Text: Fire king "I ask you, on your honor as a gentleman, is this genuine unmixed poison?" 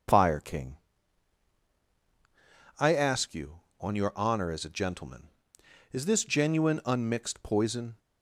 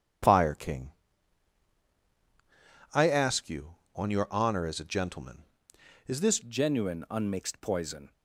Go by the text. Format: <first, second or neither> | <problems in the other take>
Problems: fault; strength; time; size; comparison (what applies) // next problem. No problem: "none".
first | pauses between "king" and "I"; strong; at 0.9 s; 2.0 s long; strong in the first // changes voice at "genuine"; from 6.4 s on; 1.7 s long